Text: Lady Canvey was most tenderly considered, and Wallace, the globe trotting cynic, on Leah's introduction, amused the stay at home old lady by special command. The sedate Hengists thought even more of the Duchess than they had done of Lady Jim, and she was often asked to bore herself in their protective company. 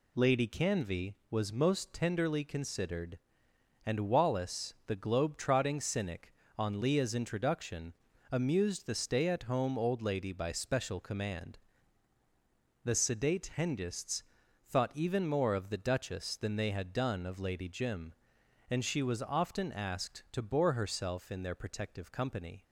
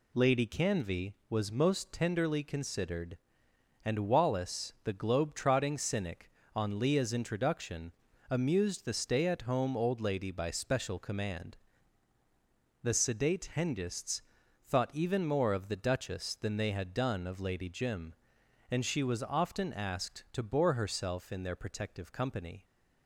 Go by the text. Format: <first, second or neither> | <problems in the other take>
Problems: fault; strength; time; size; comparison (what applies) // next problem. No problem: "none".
neither | pauses between "Hengists" and "thought"; the same in both